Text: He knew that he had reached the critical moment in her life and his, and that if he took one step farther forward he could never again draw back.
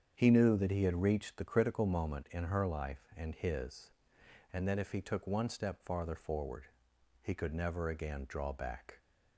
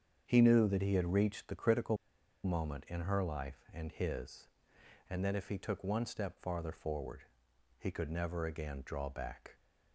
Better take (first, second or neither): first